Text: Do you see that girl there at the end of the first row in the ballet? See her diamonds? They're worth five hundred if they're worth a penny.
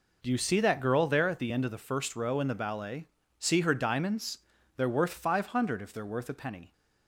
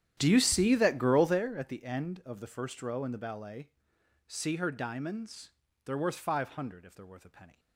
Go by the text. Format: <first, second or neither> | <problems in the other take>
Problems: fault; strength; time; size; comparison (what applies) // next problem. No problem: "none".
first | starts louder than the rest; strong; until 1.4 s; 10.5 dB